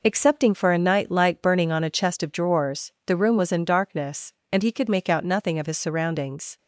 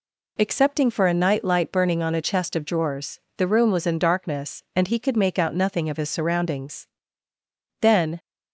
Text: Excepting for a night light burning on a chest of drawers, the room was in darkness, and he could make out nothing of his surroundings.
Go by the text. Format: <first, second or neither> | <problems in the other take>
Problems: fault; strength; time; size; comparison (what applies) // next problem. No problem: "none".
first | goes on to say "Then"; slight; from 7.8 s on; 0.38 s long